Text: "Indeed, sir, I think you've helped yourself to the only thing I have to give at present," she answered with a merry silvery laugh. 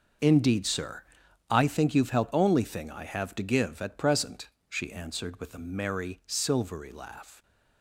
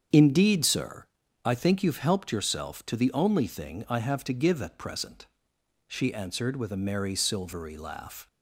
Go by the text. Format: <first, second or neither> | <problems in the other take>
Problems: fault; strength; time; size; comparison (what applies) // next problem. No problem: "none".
second | starts louder than the rest; until 1.6 s; 6.5 dB; strong in the second // skips "yourself to the"; at 2.3 s